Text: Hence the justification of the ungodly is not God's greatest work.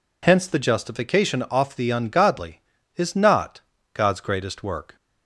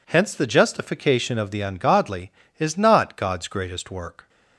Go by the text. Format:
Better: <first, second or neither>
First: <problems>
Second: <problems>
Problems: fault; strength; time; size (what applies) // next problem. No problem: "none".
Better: second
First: says "off" for "of"; at 1.4 s // pauses between "not" and "God's"; slight; at 3.5 s; 0.32 s long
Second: none